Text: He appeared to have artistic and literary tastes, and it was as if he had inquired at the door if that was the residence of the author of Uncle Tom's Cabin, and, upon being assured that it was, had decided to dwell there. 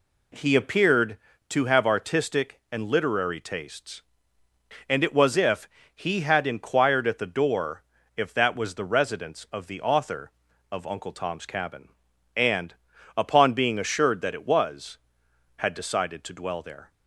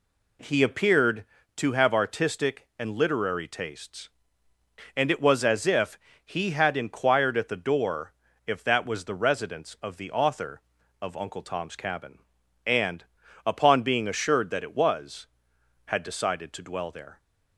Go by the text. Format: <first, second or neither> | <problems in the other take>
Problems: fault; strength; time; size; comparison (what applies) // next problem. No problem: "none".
second | skips "as"; at 5.3 s // pauses between "if" and "he"; slight; at 5.6 s; 0.26 s long; slight in the second // pauses between "door" and "if"; slight; at 7.8 s; 0.34 s long; slight in the second